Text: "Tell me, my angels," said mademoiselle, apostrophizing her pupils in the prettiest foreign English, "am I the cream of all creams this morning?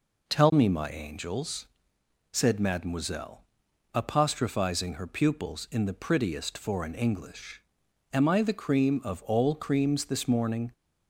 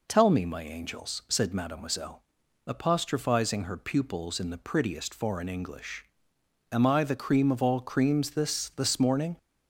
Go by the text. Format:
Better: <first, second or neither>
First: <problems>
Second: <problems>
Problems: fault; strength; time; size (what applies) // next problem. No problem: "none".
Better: first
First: none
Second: says "this" twice; at 8.6 s